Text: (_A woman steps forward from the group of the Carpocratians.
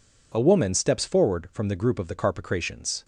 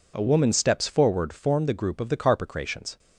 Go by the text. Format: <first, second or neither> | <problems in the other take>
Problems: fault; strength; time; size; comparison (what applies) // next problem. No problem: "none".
first | says "form" for "from"; at 1.3 s